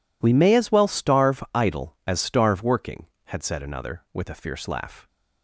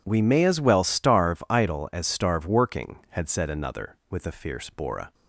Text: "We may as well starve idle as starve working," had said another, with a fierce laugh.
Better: first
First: none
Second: says "bora" for "laugh"; at 4.6 s

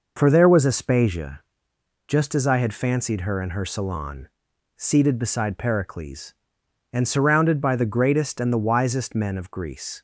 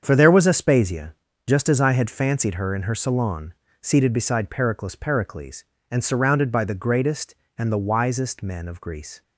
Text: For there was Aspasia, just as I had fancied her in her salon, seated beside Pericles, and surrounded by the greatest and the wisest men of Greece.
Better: first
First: none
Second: starts louder than the rest; strong; until 1.0 s; 7.5 dB // says "Pericles" twice; at 4.9 s

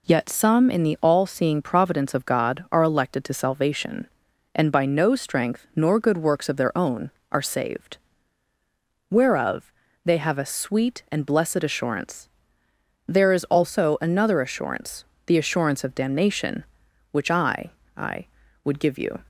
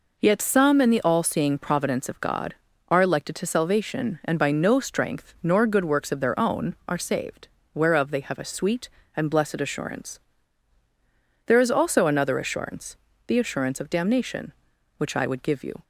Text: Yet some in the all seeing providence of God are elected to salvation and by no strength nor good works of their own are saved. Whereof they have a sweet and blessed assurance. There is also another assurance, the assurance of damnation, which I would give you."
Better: second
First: pauses between "Whereof" and "they"; slight; at 9.7 s; 0.32 s long // says "I" twice; at 17.9 s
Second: none

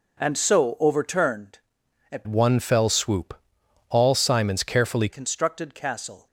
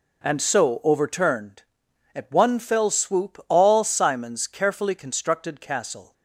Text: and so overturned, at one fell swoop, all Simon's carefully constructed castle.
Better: second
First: changes voice from "one" to "carefully"; from 2.2 to 5.0 s; 2.8 s long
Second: none

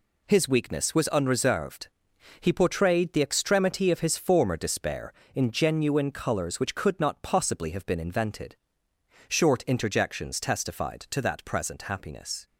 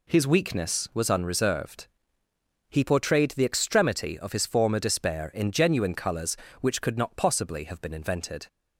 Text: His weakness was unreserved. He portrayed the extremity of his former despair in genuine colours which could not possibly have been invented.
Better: second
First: goes on to say "Short interjections testified to that present happiness"; strong; from 9.2 s on; 3.1 s long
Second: none

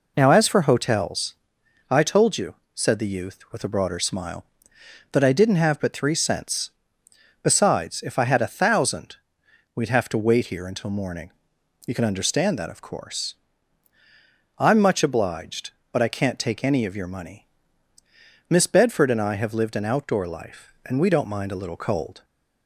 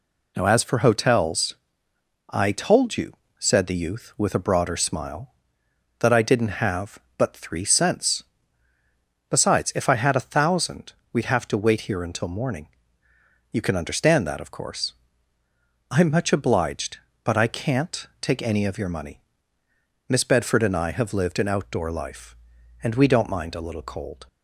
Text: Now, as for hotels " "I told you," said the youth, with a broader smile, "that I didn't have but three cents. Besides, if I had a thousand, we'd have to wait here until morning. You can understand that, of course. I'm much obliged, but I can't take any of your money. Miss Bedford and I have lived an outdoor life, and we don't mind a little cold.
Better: neither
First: none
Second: none

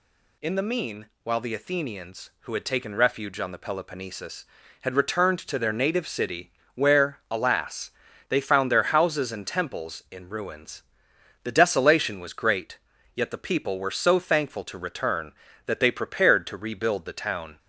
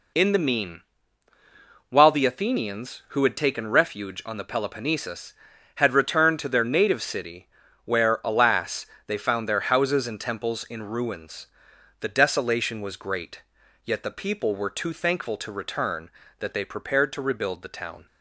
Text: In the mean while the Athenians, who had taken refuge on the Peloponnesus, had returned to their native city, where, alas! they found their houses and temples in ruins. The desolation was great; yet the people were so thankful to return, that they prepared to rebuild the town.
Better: first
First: pauses between "mean" and "while"; slight; at 1.0 s; 0.18 s long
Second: pauses between "mean" and "while"; at 0.8 s; 1.1 s long // says "too" for "so"; at 14.6 s

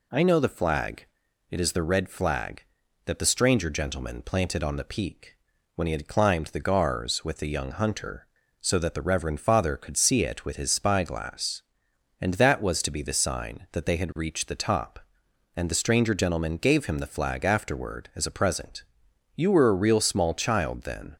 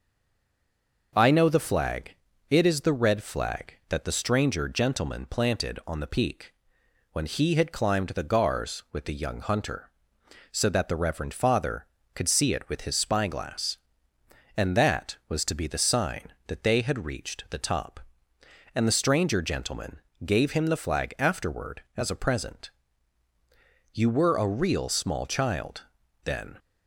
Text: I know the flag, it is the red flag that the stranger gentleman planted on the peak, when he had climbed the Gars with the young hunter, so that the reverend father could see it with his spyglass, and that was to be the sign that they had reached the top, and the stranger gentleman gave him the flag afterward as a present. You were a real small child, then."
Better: first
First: none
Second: stays silent before the first word; until 1.1 s; 1.1 s long // pauses between "gentleman" and "gave"; slight; at 19.9 s; 0.26 s long

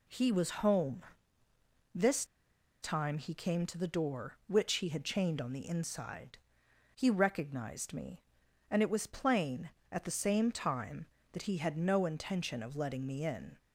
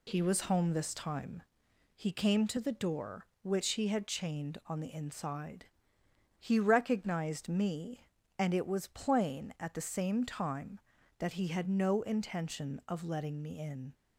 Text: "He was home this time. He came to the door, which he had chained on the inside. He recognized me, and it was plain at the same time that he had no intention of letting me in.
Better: second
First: pauses between "home" and "this"; noticeable; at 1.0 s; 0.94 s long // pauses between "this" and "time"; noticeable; at 2.2 s; 0.55 s long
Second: none

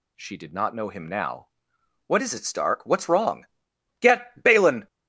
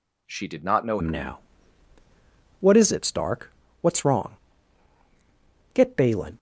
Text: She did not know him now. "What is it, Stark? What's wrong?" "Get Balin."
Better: first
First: none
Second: changes voice at "him"; from 1.0 s on; 5.3 s long

